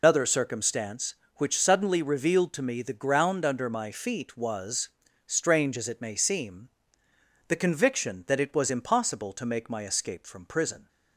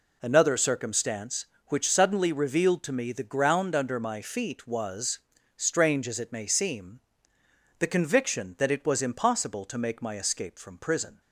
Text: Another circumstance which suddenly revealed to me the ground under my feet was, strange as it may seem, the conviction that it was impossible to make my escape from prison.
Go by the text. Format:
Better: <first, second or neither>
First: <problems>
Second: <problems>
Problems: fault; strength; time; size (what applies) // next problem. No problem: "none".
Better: second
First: loses the start of "Another"; at 0.0 s; 135 ms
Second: none